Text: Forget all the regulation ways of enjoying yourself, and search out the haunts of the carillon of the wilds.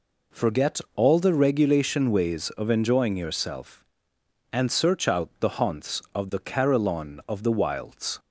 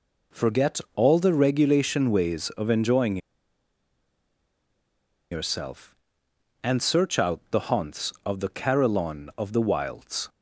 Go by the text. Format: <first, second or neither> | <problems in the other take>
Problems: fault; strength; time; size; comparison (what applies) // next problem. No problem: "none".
first | pauses between "Forget" and "all"; slight; at 0.7 s; 0.16 s long; slight in the first // pauses between "enjoying" and "yourself"; strong; at 3.1 s; 2.1 s long